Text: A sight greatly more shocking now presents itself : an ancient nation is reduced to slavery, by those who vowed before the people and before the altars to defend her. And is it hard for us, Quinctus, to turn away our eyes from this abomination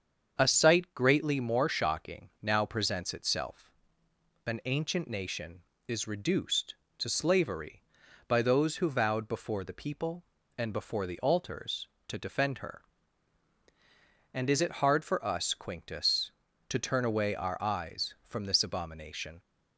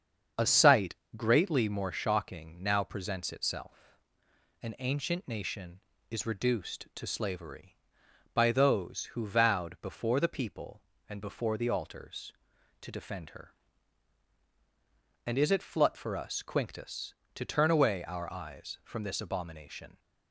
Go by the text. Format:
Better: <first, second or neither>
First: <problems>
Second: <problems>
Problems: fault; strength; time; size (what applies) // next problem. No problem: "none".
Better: first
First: starts louder than the rest; strong; until 1.3 s; 7 dB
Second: starts louder than the rest; strong; until 1.5 s; 7 dB // pauses between "sight" and "greatly"; slight; at 0.9 s; 0.20 s long // says "flut" for "hard"; at 15.6 s